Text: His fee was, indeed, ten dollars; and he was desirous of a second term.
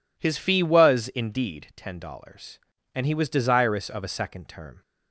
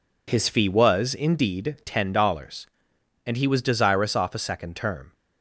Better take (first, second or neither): first